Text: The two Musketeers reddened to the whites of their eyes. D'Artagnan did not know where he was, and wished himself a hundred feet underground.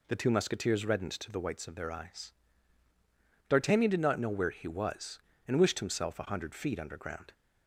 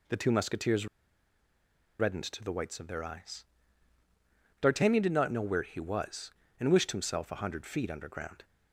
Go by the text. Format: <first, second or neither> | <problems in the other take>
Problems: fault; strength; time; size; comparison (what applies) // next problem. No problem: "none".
first | pauses between "Musketeers" and "reddened"; at 0.8 s; 1.1 s long